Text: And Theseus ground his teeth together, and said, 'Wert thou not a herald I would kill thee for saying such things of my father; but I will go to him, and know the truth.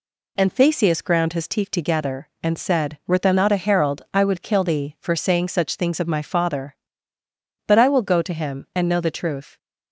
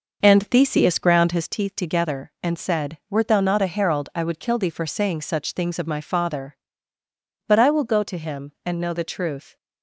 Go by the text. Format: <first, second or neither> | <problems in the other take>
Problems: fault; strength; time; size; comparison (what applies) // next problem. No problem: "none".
first | starts louder than the rest; noticeable; until 1.5 s; 5.5 dB